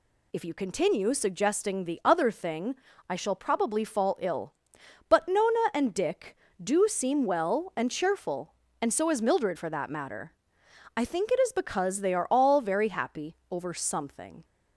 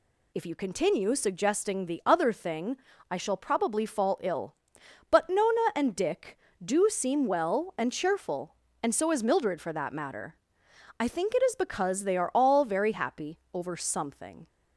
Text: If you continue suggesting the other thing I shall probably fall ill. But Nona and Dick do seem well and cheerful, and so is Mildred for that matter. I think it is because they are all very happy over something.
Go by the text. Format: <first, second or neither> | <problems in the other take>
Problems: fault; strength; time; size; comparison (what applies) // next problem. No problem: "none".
neither | pauses between "thing" and "I"; slight; the same in both // pauses between "happy" and "over"; slight; the same in both